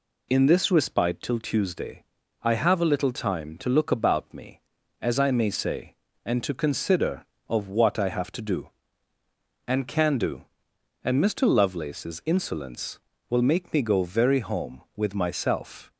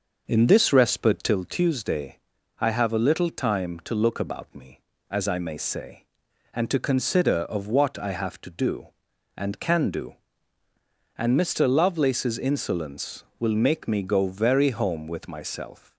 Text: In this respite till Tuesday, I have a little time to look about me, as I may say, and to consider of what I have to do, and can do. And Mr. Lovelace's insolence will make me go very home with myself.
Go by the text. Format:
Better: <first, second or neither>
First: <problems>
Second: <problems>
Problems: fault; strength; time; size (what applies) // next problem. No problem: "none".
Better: first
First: none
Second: starts louder than the rest; noticeable; until 1.4 s; 6 dB